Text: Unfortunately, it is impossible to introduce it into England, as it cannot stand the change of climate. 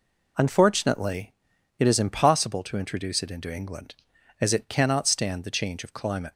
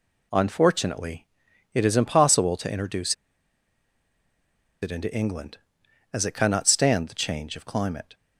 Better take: first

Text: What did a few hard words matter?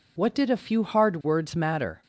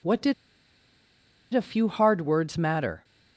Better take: first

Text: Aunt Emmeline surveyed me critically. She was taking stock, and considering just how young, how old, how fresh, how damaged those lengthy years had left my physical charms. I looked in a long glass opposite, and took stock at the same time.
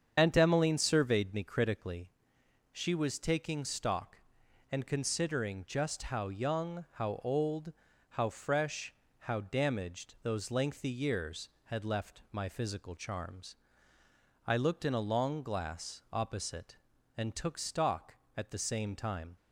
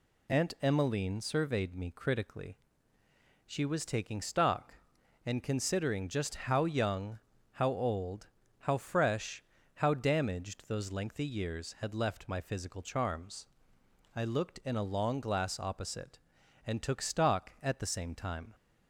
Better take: second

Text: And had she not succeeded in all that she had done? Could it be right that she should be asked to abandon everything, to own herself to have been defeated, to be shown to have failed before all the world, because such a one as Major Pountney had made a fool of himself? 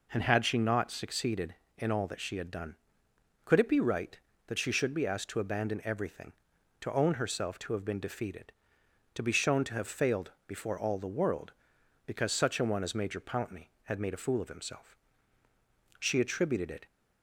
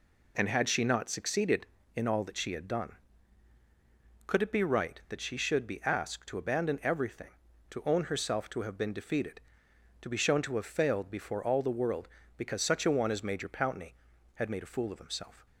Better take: second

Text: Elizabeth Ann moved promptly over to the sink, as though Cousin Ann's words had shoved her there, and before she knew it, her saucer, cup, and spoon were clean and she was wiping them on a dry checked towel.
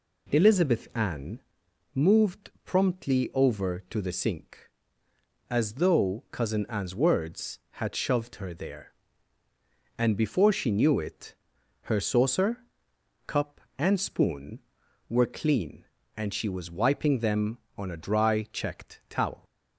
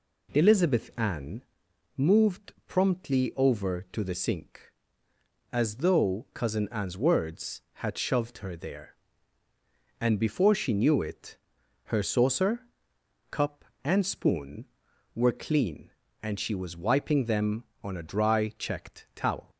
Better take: neither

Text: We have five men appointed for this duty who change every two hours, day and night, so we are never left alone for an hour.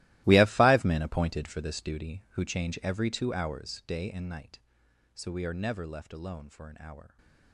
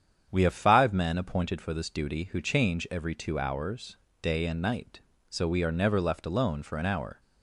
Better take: second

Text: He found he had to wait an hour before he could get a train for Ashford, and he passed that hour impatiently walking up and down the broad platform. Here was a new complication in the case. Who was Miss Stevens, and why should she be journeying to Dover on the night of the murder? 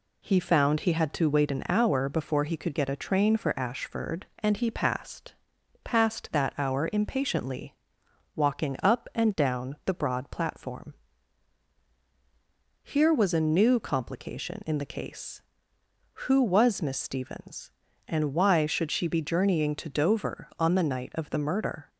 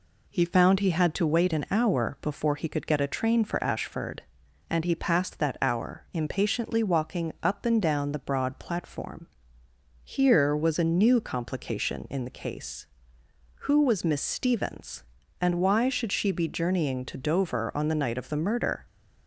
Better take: second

